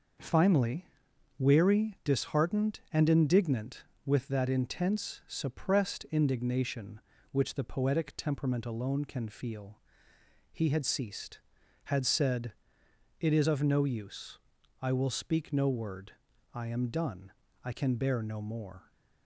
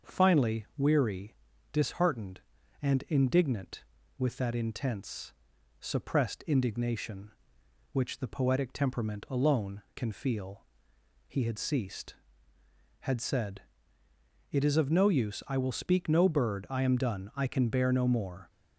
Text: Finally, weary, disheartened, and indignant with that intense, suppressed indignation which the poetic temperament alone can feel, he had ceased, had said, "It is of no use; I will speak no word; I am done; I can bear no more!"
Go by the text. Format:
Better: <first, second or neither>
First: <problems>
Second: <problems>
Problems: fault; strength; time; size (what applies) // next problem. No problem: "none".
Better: first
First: none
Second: starts louder than the rest; until 1.1 s; 6 dB // says "bird" for "word"; at 16.2 s